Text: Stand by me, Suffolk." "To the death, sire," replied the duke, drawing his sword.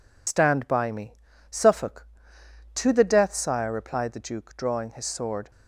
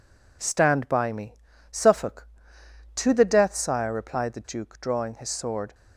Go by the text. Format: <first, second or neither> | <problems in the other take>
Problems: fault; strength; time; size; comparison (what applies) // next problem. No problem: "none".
second | loses the start of "Stand"; at 0.2 s; 70 ms